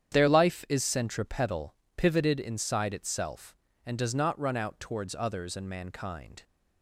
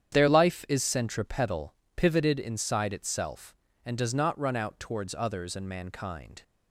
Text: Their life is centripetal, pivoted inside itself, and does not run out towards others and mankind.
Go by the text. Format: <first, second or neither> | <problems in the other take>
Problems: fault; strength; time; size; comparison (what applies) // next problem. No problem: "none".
neither | starts louder than the rest; strong; the same in both